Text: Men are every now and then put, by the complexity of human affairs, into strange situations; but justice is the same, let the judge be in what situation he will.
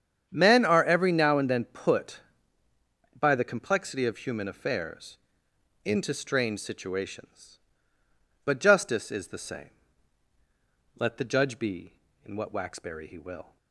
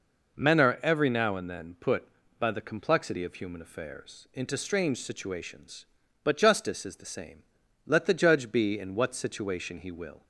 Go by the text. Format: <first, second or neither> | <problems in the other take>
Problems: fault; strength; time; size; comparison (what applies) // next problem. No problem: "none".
second | starts louder than the rest; strong; until 1.3 s; 8.5 dB // says "waxberry" for "situation"; at 12.5 s